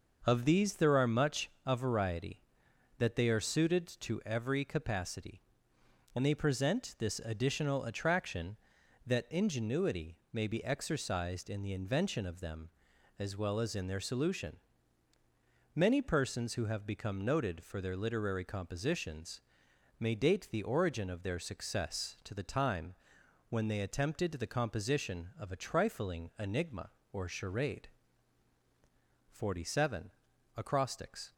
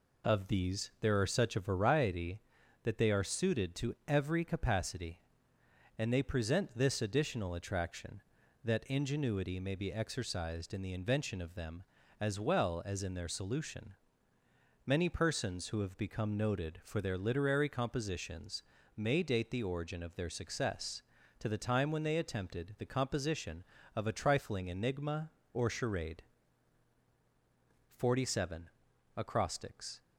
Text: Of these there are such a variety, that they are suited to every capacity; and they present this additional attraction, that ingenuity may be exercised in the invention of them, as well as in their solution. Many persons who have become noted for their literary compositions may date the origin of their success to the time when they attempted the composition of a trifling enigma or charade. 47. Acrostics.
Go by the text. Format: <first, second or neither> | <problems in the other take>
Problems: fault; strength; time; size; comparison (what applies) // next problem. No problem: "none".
second | starts louder than the rest; noticeable; until 1.2 s; 6 dB // says "much" for "such"; at 1.0 s // pauses between "ingenuity" and "may"; slight; at 10.1 s; 0.16 s long // pauses between "compositions" and "may"; noticeable; at 19.4 s; 0.58 s long; slight in the second // pauses between "time" and "when"; noticeable; at 22.9 s; 0.56 s long